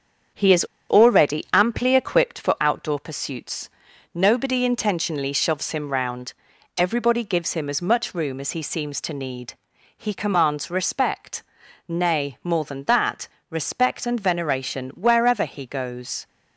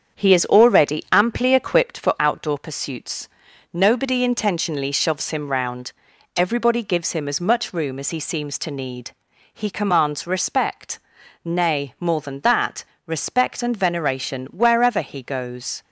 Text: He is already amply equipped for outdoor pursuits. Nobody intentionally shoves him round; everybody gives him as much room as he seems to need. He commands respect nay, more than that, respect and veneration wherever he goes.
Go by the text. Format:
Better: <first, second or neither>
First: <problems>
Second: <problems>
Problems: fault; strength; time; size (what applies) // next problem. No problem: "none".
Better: second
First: starts louder than the rest; strong; until 1.6 s; 7.5 dB // pauses between "is" and "already"; slight; at 0.6 s; 0.25 s long // pauses between "respect" and "nay"; at 11.4 s; 0.44 s long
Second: starts louder than the rest; strong; until 1.2 s; 7.5 dB // pauses between "respect" and "nay"; at 10.9 s; 0.44 s long